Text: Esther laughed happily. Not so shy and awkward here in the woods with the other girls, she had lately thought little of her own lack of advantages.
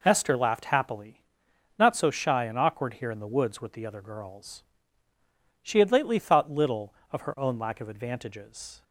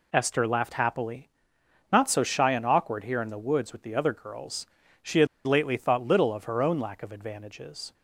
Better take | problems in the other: first | pauses between "had" and "lately"; slight; at 5.2 s; 0.20 s long

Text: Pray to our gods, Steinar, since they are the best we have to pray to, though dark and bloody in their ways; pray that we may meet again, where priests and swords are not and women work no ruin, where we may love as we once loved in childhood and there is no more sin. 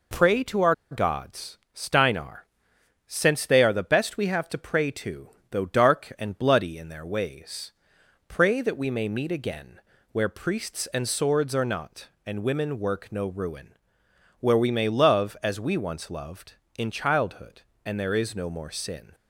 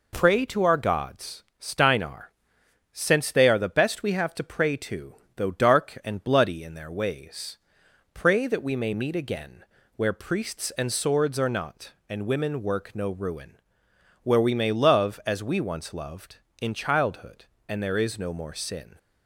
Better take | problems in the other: second | pauses between "our" and "gods"; slight; at 0.7 s; 0.16 s long

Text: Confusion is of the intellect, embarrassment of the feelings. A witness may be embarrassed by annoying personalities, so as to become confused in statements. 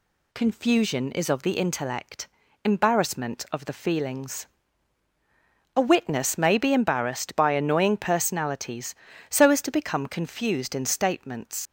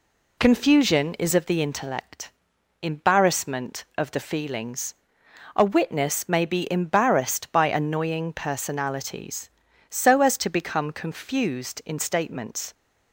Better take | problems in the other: second | leaves "statements" unfinished; at 11.6 s; 95 ms

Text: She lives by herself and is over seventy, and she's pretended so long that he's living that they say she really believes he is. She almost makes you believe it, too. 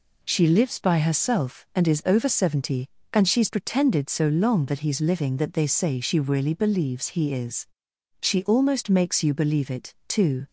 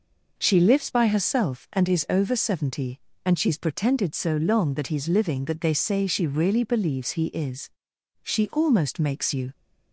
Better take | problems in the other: first | stops before "believe it too"; at 9.5 s

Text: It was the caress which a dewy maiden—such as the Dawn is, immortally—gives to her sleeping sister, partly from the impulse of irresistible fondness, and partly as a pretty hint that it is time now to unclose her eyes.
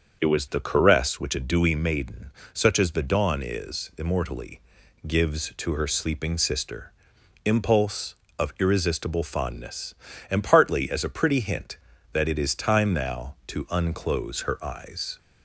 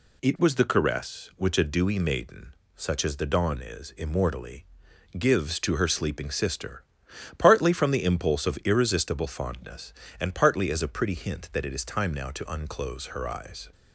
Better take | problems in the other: second | starts louder than the rest; until 1.2 s; 6.5 dB // skips "partly from the"; at 7.1 s

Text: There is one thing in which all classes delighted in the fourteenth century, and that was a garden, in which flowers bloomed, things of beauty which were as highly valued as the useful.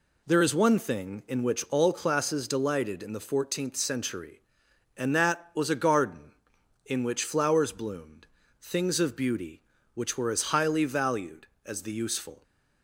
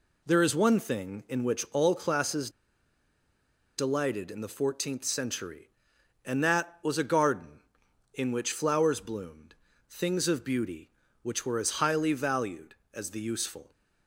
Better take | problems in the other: first | pauses between "classes" and "delighted"; strong; at 2.4 s; 1.2 s long

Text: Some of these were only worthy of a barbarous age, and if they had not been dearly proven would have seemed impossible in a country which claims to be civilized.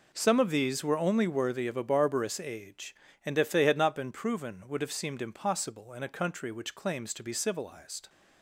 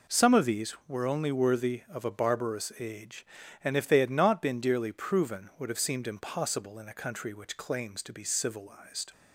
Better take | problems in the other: second | skips "dearly"; at 4.1 s

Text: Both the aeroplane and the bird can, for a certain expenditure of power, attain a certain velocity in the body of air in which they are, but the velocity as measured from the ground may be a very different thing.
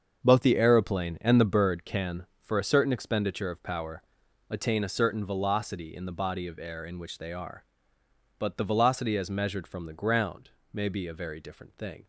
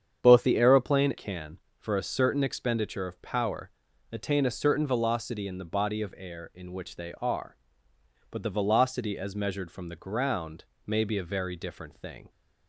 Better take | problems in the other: first | starts louder than the rest; strong; until 1.2 s; 8 dB; also in the first // skips "and the bird"; at 1.1 s // pauses between "ground" and "may"; slight; at 10.6 s; 0.22 s long; slight in the first

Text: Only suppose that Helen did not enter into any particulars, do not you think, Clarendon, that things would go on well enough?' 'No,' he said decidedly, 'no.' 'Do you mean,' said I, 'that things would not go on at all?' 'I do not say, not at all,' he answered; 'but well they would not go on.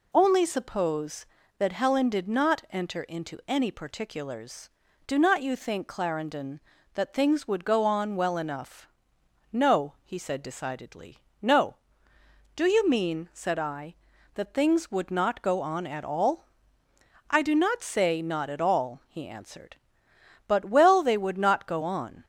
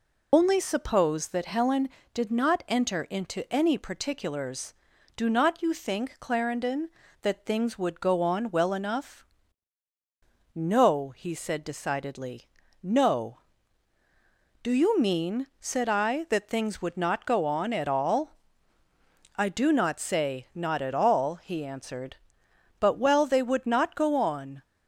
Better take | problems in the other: first | loses the start of "Only"; at 0.3 s; 60 ms

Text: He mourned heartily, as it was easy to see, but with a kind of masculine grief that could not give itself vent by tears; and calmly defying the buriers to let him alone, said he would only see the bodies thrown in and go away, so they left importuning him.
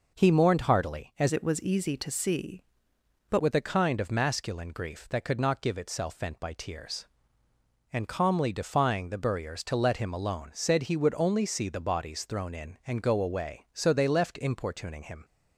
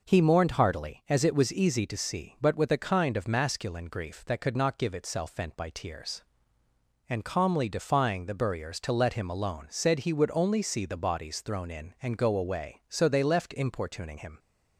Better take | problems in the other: second | changes voice from "it" to "but"; from 1.3 to 3.3 s; 2.0 s long

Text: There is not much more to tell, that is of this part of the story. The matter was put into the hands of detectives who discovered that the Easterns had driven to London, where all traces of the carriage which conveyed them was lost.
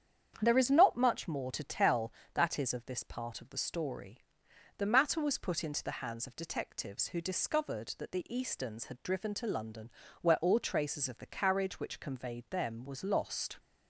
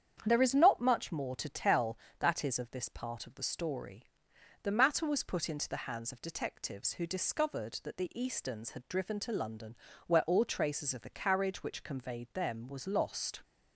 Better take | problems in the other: neither | starts louder than the rest; strong; the same in both

